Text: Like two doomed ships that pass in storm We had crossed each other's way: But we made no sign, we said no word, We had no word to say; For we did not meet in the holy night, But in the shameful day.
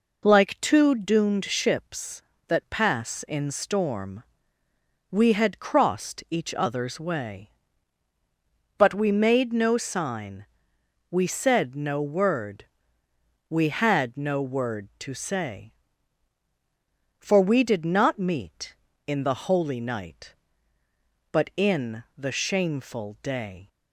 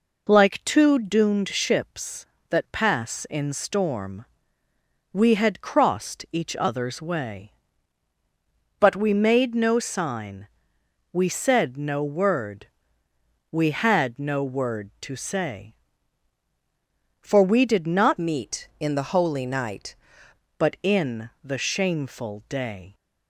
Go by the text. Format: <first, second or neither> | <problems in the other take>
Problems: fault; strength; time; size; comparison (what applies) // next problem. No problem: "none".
first | pauses between "storm" and "We"; noticeable; at 4.2 s; 0.88 s long; noticeable in the first // changes voice from "meet" to "night"; from 18.1 to 19.9 s; 1.8 s long // pauses between "in" and "the"; slight; at 21.2 s; 0.16 s long; slight in the first